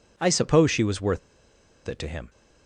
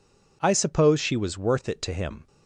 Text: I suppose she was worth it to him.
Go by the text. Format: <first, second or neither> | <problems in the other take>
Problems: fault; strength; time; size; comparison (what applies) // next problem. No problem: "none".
second | pauses between "worth" and "it"; noticeable; at 1.1 s; 0.68 s long